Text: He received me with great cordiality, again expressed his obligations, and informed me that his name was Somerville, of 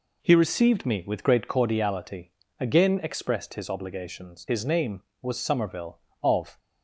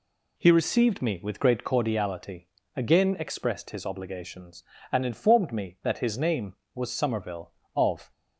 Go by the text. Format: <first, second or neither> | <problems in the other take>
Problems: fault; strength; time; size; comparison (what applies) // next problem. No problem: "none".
second | skips "and informed me that"; at 4.4 s